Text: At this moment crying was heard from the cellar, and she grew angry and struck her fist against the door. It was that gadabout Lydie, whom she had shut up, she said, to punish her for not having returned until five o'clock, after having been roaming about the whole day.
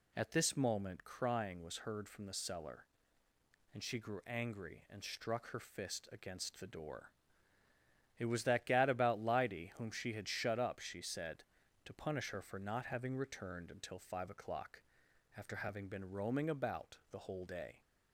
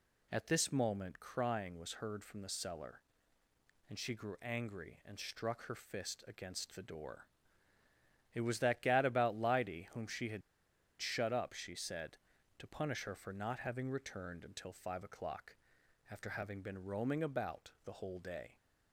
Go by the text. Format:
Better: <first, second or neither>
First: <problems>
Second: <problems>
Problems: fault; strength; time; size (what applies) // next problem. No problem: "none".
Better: first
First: none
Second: pauses between "had" and "shut"; noticeable; at 10.4 s; 0.60 s long